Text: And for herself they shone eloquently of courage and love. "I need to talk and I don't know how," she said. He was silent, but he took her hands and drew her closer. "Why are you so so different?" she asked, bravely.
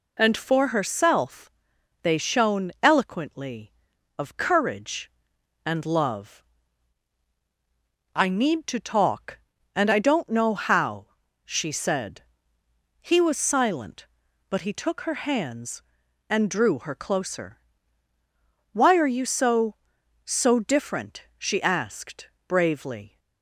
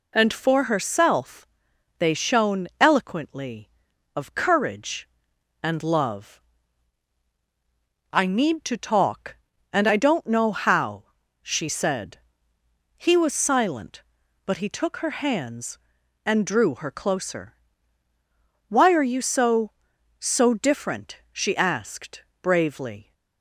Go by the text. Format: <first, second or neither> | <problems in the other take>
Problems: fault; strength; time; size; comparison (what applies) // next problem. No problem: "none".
neither | pauses between "herself" and "they"; noticeable; the same in both